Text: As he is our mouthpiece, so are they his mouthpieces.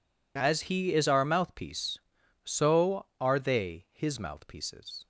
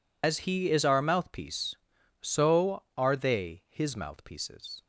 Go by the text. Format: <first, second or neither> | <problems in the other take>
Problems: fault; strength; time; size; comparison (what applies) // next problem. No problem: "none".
first | loses the start of "As"; at 0.2 s; 110 ms